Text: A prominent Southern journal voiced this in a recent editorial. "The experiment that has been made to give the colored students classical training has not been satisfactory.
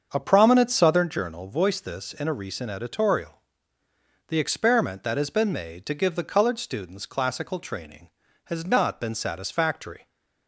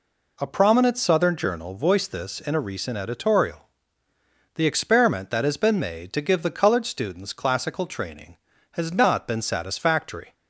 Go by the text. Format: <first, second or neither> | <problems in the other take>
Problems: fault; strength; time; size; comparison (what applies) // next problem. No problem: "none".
second | starts louder than the rest; until 1.1 s; 7 dB